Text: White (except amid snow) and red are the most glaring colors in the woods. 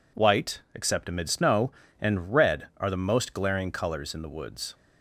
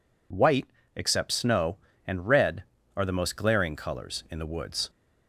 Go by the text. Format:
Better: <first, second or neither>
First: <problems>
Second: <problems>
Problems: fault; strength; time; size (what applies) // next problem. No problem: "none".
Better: first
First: none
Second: skips "amid"; at 1.3 s